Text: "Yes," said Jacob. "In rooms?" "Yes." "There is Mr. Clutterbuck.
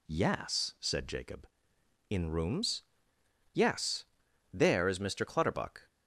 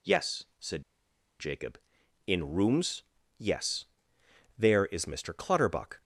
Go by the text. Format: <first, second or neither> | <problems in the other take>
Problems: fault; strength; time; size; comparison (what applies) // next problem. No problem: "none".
first | pauses between "said" and "Jacob"; noticeable; at 0.8 s; 0.57 s long